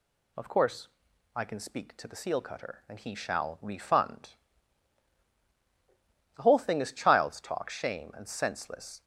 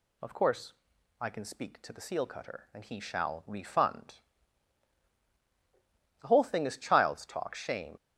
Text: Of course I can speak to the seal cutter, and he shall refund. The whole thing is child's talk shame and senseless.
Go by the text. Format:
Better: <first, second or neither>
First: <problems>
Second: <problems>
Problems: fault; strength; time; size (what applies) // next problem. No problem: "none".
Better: first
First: pauses between "course" and "I"; noticeable; at 0.8 s; 0.48 s long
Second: pauses between "course" and "I"; noticeable; at 0.7 s; 0.48 s long // stops before "and senseless"; at 7.9 s